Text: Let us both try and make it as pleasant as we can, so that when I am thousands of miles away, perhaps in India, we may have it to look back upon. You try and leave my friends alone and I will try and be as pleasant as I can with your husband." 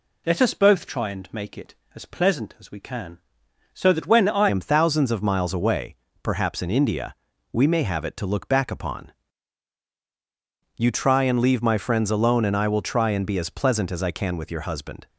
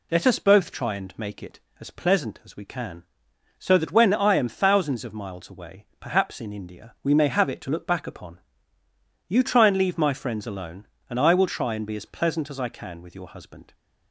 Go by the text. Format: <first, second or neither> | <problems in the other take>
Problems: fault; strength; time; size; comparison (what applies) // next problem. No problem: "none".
second | changes voice at "am"; from 4.4 s on; 10.6 s long